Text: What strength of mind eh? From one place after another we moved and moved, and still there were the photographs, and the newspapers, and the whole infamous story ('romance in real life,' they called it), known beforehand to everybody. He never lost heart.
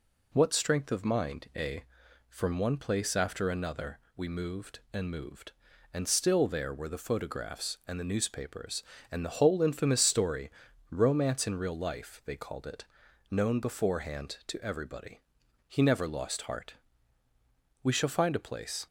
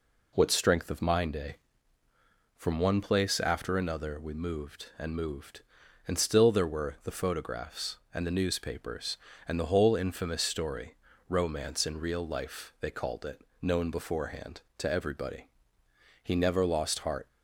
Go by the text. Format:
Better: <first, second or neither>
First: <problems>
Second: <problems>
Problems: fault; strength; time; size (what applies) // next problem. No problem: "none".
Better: second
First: pauses between "another" and "we"; slight; at 3.9 s; 0.18 s long // goes on to say "We shall find a place"; noticeable; from 17.8 s on; 1.0 s long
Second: none